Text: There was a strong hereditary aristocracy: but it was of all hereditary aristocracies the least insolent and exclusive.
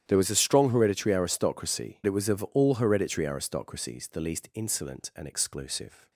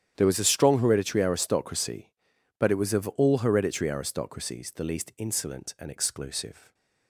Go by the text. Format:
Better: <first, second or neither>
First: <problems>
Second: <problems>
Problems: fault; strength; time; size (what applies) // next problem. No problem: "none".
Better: second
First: starts louder than the rest; strong; until 1.0 s; 10.5 dB // skips "but"; at 2.0 s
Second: starts louder than the rest; strong; until 1.1 s; 10 dB